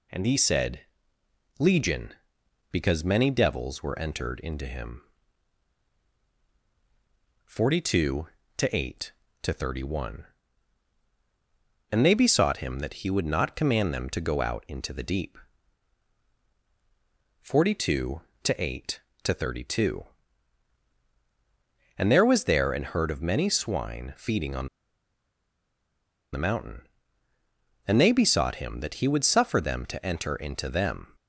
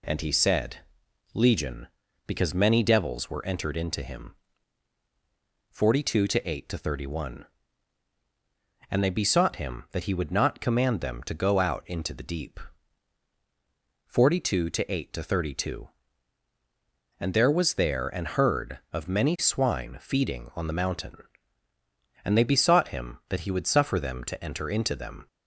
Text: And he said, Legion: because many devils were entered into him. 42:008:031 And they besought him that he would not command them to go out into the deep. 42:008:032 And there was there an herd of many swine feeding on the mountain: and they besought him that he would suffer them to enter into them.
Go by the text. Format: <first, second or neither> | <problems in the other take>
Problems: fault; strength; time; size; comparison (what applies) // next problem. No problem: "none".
second | pauses between "on" and "the"; strong; at 24.6 s; 1.6 s long